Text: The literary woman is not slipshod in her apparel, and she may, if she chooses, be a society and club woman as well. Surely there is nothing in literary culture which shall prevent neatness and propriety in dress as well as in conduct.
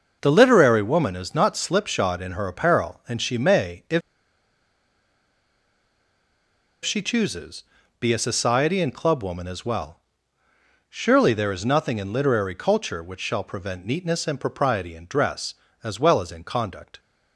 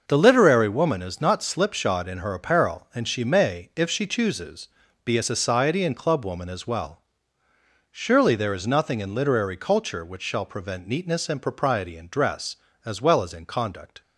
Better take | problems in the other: second | starts louder than the rest; noticeable; until 1.2 s; 6 dB; noticeable in the second // pauses between "if" and "she"; strong; at 4.0 s; 2.8 s long

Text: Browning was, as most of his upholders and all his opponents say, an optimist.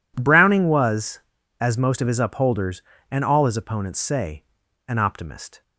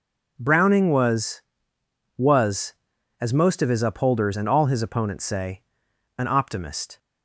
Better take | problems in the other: first | says "was" twice; at 2.1 s

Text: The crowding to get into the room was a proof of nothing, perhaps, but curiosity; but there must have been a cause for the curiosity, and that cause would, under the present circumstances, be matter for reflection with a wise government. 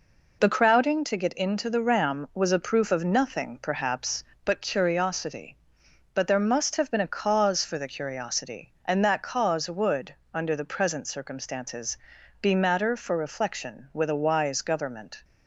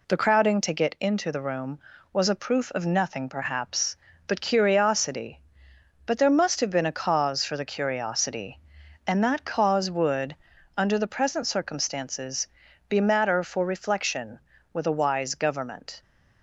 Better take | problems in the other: second | says "ram" for "room"; at 1.8 s

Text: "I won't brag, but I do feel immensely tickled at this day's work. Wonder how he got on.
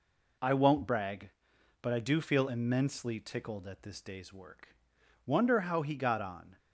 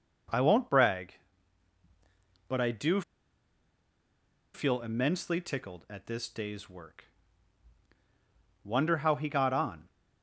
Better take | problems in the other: first | pauses between "do" and "feel"; strong; at 3.0 s; 1.5 s long

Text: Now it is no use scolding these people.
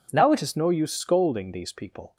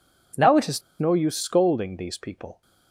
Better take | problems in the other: first | pauses between "is" and "no"; slight; at 0.8 s; 0.17 s long

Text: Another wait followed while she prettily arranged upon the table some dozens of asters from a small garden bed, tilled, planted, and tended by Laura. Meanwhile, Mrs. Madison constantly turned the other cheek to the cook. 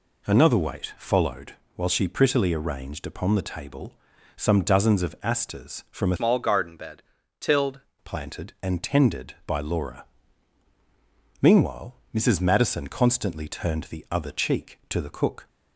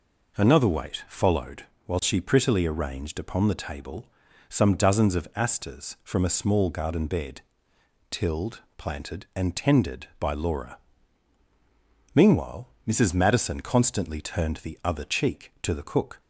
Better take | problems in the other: second | pauses between "followed" and "while"; slight; at 1.5 s; 0.22 s long; slight in the second // pauses between "table" and "some"; at 3.9 s; 0.42 s long; also in the second // changes voice from "small" to "tilled"; from 6.1 to 7.7 s; 1.6 s long

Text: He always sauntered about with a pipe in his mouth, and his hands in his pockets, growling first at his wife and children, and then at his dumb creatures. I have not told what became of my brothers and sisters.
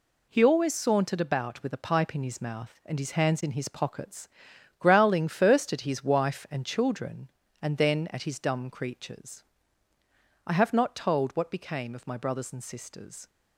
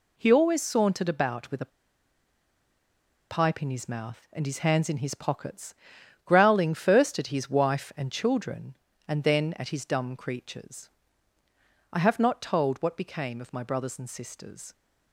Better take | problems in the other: first | pauses between "a" and "pipe"; strong; at 1.7 s; 1.6 s long

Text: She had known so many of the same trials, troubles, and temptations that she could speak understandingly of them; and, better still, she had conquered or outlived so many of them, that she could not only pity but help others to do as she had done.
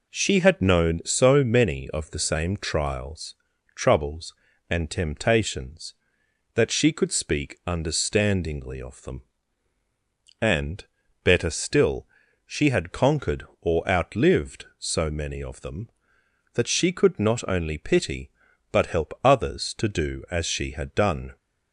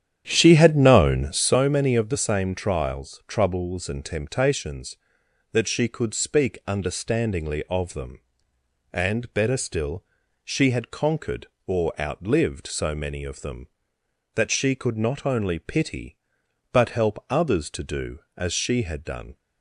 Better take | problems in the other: first | starts louder than the rest; strong; until 1.6 s; 9.5 dB

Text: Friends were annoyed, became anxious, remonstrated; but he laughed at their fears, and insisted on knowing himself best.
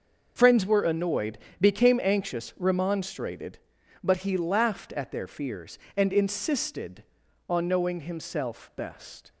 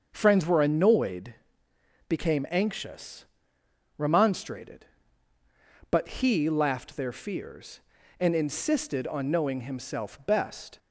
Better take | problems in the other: first | starts louder than the rest; until 1.1 s; 6.5 dB; also in the first // skips "at"; at 6.9 s

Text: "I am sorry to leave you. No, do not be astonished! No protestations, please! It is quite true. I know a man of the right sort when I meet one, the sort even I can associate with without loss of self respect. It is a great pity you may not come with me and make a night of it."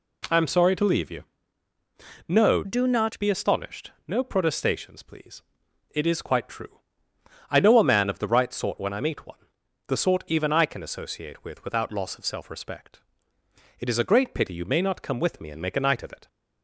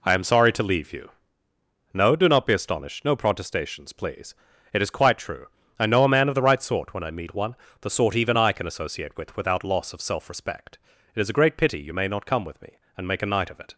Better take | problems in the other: second | changes voice from "do" to "not"; from 2.6 to 3.1 s; 0.5 s long

